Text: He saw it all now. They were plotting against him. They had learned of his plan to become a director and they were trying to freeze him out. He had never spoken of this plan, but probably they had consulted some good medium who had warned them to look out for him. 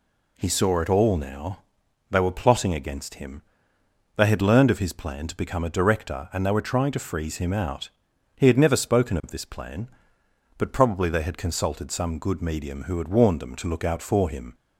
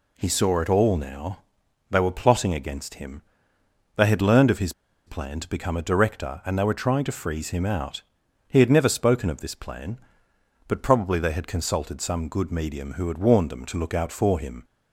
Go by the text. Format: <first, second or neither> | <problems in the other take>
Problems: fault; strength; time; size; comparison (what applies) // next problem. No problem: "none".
first | pauses between "his" and "plan"; slight; at 4.7 s; 0.35 s long